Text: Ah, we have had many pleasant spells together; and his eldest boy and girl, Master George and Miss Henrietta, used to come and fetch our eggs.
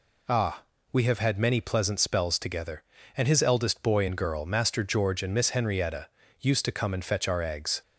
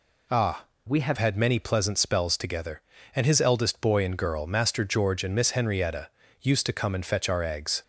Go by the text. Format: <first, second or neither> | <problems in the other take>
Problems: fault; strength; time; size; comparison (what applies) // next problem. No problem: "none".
first | changes voice from "we" to "have"; from 0.8 to 1.1 s; 0.3 s long